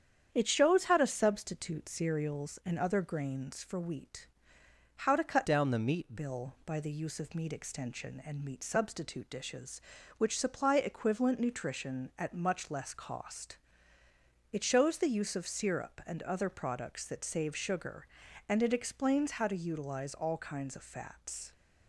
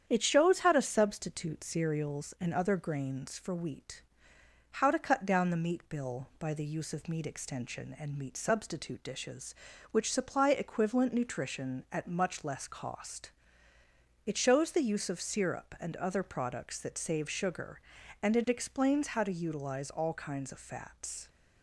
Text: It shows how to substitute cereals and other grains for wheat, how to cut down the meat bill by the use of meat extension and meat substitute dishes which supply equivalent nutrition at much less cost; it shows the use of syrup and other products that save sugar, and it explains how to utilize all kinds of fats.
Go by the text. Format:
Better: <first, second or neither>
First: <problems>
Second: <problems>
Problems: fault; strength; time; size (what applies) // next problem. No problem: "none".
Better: second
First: starts louder than the rest; strong; until 1.3 s; 8.5 dB // changes voice from "down" to "meat"; from 5.4 to 6.1 s; 0.7 s long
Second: starts louder than the rest; strong; until 1.0 s; 8.5 dB